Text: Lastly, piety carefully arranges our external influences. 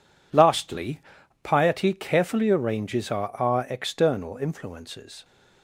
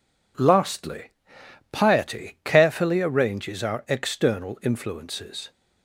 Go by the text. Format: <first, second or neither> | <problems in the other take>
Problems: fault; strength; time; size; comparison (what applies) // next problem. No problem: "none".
second | says "our" twice; at 3.3 s